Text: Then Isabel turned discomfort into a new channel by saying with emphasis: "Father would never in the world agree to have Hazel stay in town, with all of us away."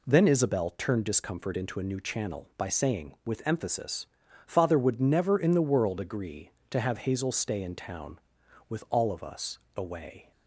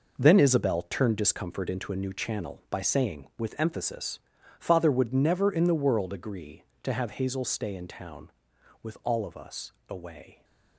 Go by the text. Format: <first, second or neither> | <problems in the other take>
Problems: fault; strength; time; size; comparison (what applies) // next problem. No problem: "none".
first | gets quieter; strong; throughout; 10 dB // pauses between "us" and "away"; slight; at 9.7 s; 0.17 s long; slight in the first